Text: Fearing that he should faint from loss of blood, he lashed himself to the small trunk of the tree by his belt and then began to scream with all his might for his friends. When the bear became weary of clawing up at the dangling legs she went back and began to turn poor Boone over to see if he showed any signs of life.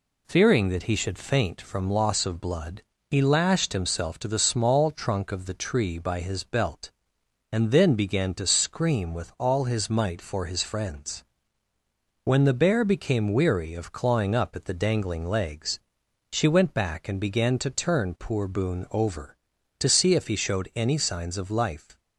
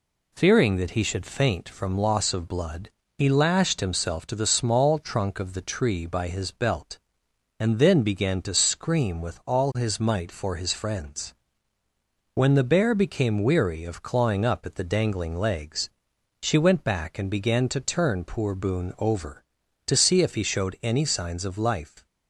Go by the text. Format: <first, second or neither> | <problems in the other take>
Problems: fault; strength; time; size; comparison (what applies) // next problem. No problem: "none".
neither | pauses between "legs" and "she"; noticeable; the same in both